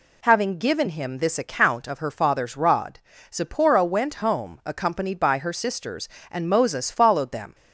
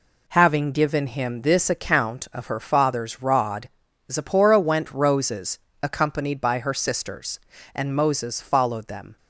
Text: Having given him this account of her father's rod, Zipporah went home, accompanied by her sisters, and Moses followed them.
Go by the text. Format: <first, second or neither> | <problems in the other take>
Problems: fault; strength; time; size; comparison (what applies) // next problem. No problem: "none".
first | says "roses" for "home"; at 4.9 s